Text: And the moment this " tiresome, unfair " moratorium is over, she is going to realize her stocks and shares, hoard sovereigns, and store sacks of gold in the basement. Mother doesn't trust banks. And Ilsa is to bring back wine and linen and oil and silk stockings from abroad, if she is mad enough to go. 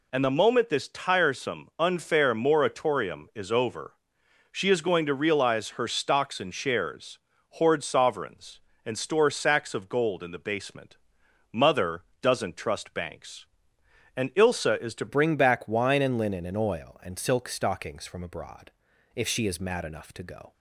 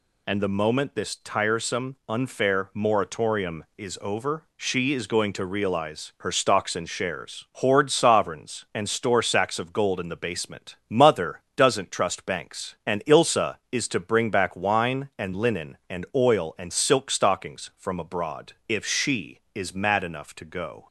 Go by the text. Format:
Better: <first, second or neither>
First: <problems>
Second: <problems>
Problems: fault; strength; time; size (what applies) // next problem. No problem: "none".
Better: second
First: pauses between "Mother" and "doesn't"; slight; at 12.0 s; 0.18 s long // changes voice at "bring"; from 15.0 s on; 5.5 s long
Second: none